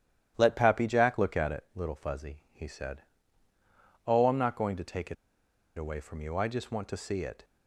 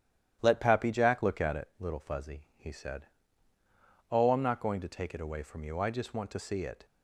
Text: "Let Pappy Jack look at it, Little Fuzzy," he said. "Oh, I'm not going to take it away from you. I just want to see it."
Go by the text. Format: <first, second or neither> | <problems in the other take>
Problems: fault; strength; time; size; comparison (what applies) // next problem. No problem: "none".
second | starts louder than the rest; strong; until 1.3 s; 11.5 dB; strong in the second // pauses between "it" and "away"; noticeable; at 5.1 s; 0.61 s long